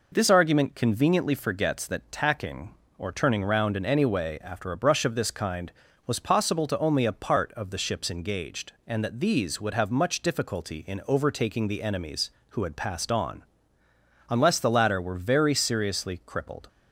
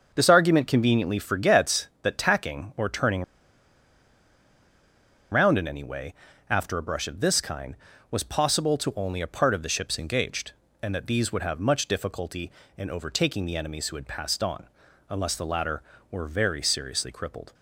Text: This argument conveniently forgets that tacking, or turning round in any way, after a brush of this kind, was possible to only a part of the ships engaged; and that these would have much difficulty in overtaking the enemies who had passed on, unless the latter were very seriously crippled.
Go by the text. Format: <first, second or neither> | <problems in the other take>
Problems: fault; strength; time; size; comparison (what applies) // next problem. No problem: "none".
first | starts louder than the rest; until 1.1 s; 6.5 dB // pauses between "turning" and "round"; strong; at 3.2 s; 2.0 s long